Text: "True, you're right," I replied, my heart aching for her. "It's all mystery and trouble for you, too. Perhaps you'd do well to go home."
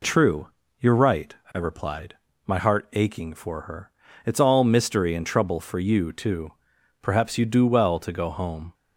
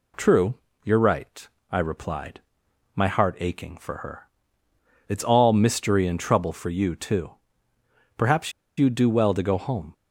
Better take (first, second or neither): first